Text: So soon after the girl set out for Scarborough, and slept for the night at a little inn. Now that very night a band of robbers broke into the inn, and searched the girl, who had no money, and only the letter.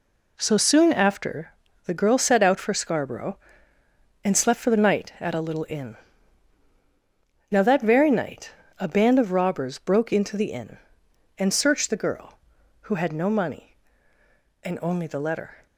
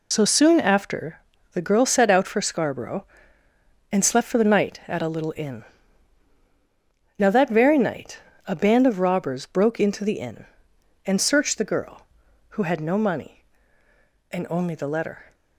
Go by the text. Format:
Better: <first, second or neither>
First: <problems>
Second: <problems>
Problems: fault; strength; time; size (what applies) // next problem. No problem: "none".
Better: first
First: pauses between "after" and "the"; slight; at 1.5 s; 0.34 s long // pauses between "night" and "a"; slight; at 8.5 s; 0.26 s long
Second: loses the start of "So"; at 0.1 s; 60 ms // pauses between "after" and "the"; slight; at 1.1 s; 0.34 s long // pauses between "night" and "a"; slight; at 8.1 s; 0.26 s long